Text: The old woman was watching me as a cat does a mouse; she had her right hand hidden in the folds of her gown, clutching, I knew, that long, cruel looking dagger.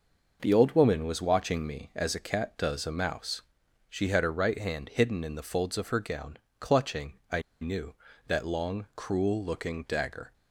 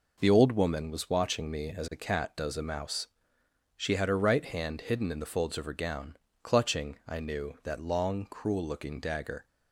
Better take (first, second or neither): second